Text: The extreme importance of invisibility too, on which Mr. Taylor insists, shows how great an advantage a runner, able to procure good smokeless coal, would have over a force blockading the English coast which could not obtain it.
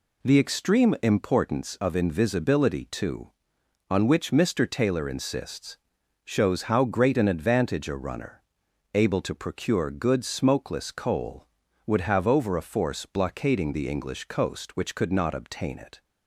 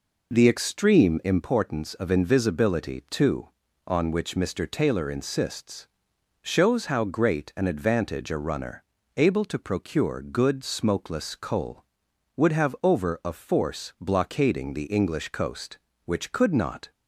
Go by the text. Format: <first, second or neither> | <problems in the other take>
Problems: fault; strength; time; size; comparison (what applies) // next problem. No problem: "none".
first | stops before "obtain it"; at 16.9 s